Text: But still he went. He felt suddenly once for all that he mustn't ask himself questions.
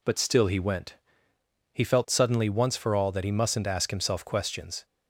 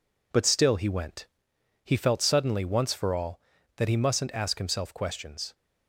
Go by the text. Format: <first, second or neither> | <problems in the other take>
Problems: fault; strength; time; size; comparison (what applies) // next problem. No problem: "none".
first | gets quieter; noticeable; throughout; 6 dB